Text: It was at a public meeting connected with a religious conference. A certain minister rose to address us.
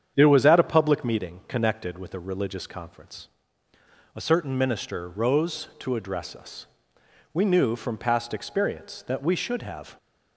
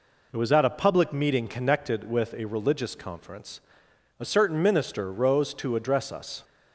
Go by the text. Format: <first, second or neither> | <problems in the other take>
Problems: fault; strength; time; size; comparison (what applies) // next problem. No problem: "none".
second | starts louder than the rest; strong; until 1.1 s; 8.5 dB // goes on to say "We knew from past experience that we should have"; strong; from 7.3 s on; 2.6 s long